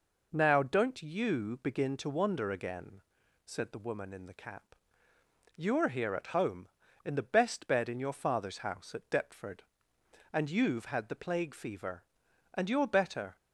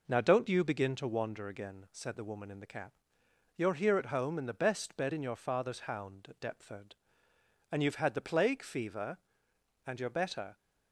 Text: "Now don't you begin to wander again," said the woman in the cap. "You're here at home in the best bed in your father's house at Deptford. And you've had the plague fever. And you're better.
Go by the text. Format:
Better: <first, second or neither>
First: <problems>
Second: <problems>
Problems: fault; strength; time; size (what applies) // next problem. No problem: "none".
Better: first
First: none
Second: says "hound" for "house"; at 5.8 s